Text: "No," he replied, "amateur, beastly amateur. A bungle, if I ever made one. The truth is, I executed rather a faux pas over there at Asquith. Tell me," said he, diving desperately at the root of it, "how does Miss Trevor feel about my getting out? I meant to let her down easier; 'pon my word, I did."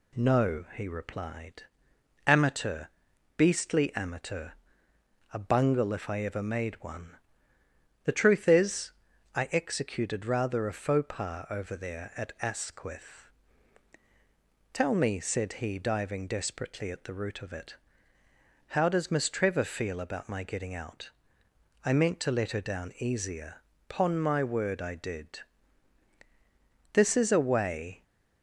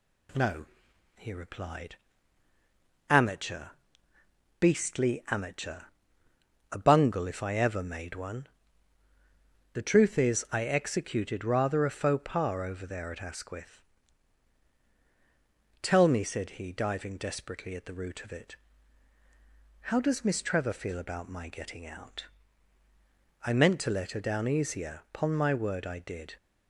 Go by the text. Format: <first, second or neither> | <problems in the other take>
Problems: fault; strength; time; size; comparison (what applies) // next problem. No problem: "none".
second | goes on to say "This is a way"; noticeable; from 26.9 s on; 1.1 s long